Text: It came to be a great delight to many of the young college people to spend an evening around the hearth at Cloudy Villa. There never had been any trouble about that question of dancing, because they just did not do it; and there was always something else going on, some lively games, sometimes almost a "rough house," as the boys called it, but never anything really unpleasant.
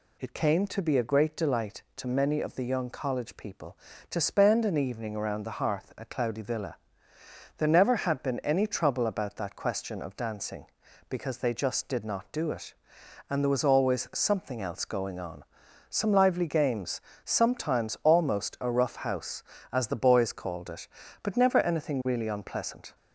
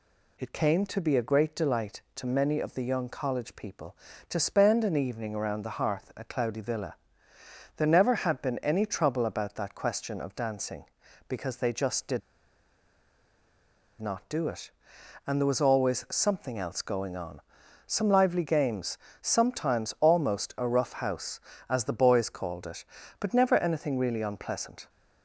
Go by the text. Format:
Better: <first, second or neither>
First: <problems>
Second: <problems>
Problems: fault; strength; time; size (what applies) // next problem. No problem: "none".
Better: first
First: none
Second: pauses between "did" and "not"; strong; at 12.2 s; 1.8 s long